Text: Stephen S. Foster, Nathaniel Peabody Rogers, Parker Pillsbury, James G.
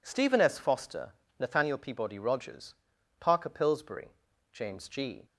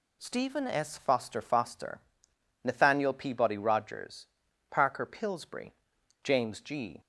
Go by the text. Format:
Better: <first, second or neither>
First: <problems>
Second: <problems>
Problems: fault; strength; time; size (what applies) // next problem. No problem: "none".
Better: first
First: none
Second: says "Foster" twice; at 1.4 s